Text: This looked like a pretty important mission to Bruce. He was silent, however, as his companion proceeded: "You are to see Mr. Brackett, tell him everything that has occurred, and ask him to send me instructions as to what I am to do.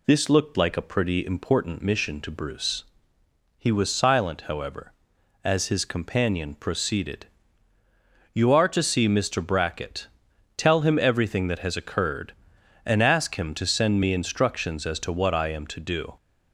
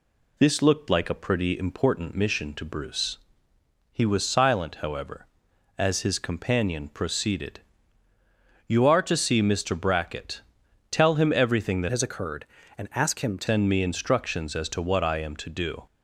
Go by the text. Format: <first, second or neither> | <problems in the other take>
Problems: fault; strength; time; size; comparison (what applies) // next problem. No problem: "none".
first | changes voice from "has" to "to"; from 11.9 to 13.4 s; 1.5 s long